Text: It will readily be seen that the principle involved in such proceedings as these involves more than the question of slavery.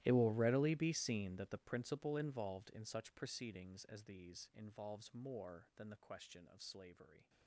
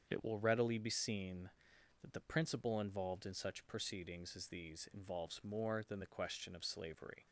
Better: second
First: gets quieter; strong; throughout; 20 dB // starts louder than the rest; strong; until 1.0 s; 15 dB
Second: starts louder than the rest; strong; until 1.1 s; 7 dB

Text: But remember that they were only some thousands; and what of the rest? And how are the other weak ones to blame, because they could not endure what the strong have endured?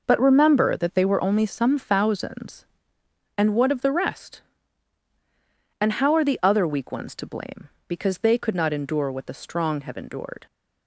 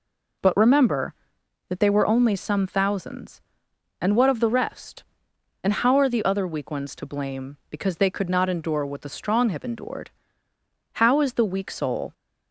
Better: first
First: none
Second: goes on to say "How is the weak soul"; noticeable; from 10.9 s on; 1.2 s long

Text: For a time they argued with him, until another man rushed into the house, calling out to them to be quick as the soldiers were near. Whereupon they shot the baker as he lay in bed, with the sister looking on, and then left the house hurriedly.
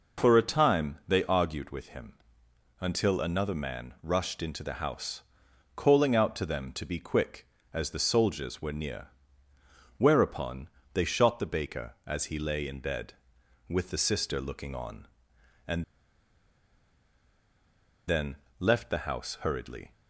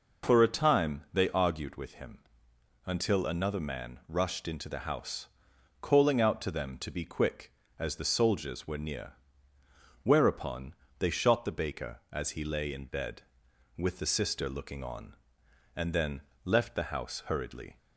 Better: second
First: pauses between "Whereupon" and "they"; slight; at 10.6 s; 0.26 s long // pauses between "and" and "then"; strong; at 15.8 s; 2.2 s long // pauses between "then" and "left"; slight; at 18.3 s; 0.24 s long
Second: pauses between "Whereupon" and "they"; slight; at 10.7 s; 0.26 s long // pauses between "then" and "left"; slight; at 16.1 s; 0.24 s long

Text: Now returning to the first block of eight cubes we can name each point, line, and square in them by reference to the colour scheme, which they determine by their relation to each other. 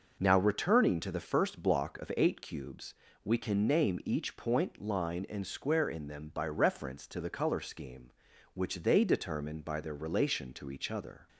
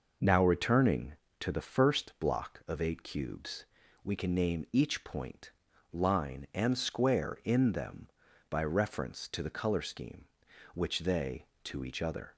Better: first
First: pauses between "cubes" and "we"; slight; at 2.9 s; 0.32 s long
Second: pauses between "cubes" and "we"; at 3.6 s; 0.40 s long // skips "determine by their relation"; at 11.5 s

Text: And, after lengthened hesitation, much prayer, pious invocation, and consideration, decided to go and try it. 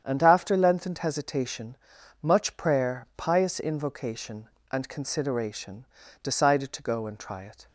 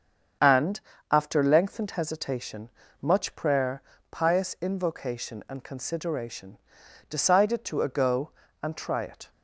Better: first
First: starts louder than the rest; strong; until 1.0 s; 8.5 dB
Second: starts louder than the rest; strong; until 1.7 s; 7.5 dB // says "ago" for "go"; at 7.8 s

